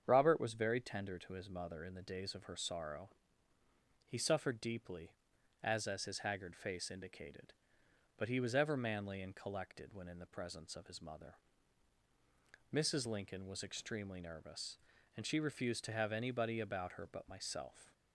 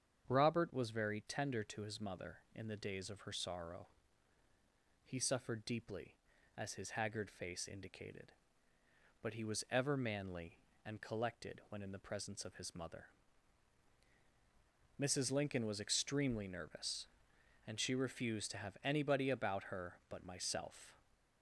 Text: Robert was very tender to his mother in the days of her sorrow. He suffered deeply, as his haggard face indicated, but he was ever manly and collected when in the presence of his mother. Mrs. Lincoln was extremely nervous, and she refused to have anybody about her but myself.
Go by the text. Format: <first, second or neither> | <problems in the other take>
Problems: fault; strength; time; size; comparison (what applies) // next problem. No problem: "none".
second | starts louder than the rest; strong; until 1.0 s; 7.5 dB; strong in the second // says "as" twice; at 5.8 s